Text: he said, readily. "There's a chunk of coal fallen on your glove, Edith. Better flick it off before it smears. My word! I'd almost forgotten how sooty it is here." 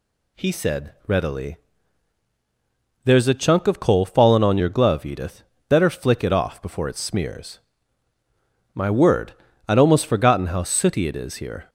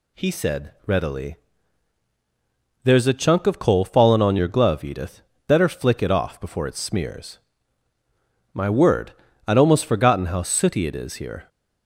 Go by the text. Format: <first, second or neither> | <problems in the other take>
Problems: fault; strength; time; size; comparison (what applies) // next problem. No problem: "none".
neither | none